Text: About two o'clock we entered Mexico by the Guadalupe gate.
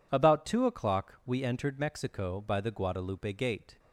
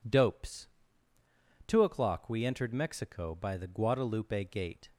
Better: first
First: none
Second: says "Dopes" for "About"; at 0.0 s

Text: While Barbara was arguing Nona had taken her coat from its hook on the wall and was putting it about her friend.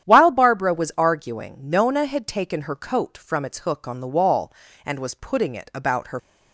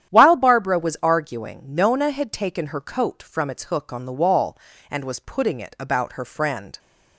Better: second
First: starts louder than the rest; strong; until 1.1 s; 10 dB // stops before "friend"; at 6.1 s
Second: starts louder than the rest; strong; until 1.1 s; 10.5 dB

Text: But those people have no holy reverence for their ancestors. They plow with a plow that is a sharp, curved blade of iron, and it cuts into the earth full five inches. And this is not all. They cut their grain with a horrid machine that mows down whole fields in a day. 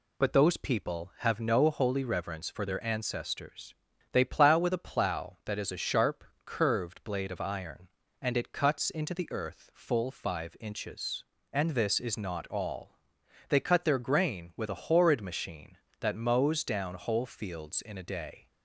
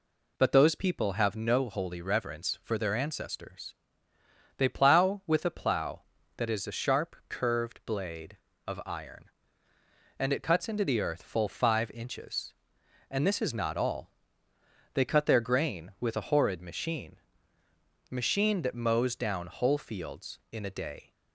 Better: first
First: none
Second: says "machine" twice; at 18.1 s

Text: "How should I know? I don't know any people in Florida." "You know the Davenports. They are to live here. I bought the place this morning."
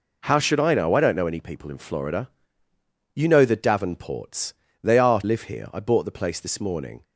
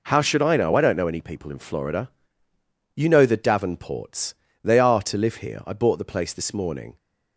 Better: second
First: skips "to"; at 5.2 s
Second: none

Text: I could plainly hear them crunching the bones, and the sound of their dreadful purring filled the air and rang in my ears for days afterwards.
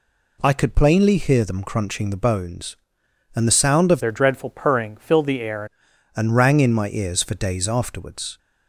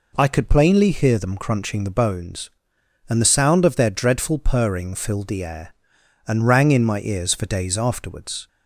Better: second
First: changes voice from "their" to "air"; from 4.0 to 5.6 s; 1.6 s long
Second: none

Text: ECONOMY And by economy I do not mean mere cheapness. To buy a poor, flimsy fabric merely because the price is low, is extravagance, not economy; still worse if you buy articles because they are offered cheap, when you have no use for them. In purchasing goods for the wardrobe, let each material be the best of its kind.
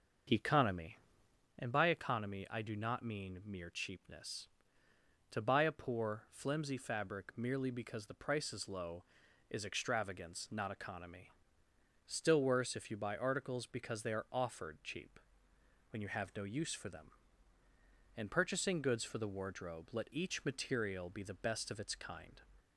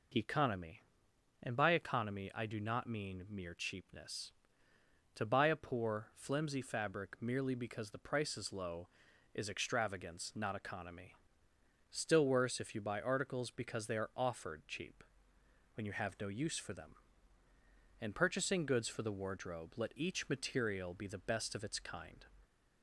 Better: second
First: starts louder than the rest; until 1.6 s; 6.5 dB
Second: none

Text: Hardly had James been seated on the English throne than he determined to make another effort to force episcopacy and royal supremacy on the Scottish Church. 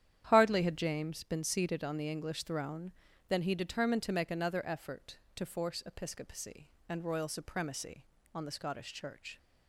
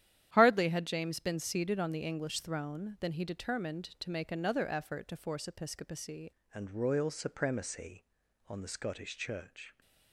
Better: first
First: starts louder than the rest; strong; until 1.3 s; 10 dB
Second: starts louder than the rest; strong; until 1.3 s; 11 dB // changes voice at "and"; from 6.5 s on; 3.2 s long

